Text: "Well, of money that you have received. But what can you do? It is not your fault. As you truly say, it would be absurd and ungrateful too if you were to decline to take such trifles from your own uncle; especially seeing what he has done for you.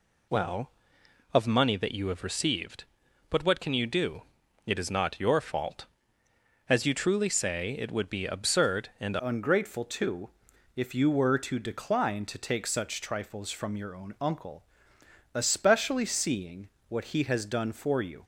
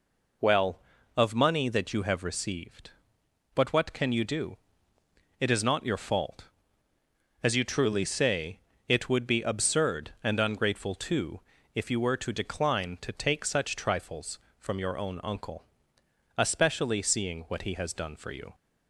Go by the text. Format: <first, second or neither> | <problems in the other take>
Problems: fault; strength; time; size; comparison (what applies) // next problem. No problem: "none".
second | changes voice at "ungrateful"; from 9.2 s on; 9.0 s long // pauses between "too" and "if"; at 10.3 s; 0.44 s long; slight in the second // pauses between "seeing" and "what"; slight; at 16.7 s; 0.18 s long